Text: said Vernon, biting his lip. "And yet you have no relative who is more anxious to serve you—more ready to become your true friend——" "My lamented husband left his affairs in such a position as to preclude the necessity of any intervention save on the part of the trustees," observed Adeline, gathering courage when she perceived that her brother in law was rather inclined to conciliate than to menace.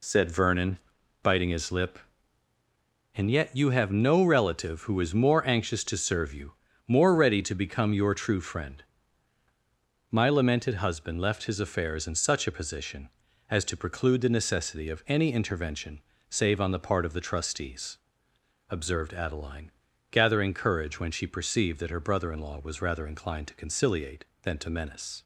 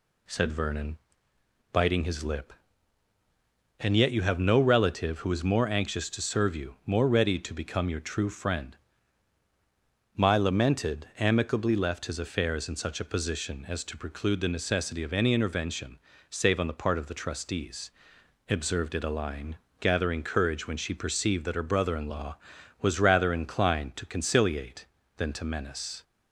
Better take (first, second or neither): first